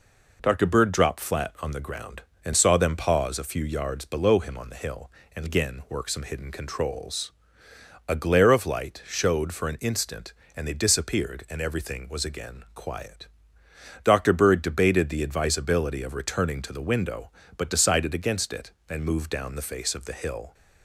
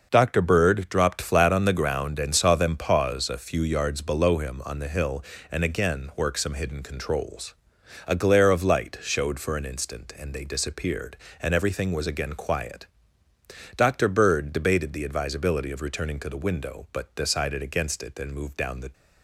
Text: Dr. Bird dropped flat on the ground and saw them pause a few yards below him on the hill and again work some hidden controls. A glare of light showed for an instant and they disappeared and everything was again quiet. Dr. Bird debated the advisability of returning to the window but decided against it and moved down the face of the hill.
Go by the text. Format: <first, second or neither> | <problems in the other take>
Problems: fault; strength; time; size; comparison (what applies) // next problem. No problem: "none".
first | stops before "face of the hill"; at 18.9 s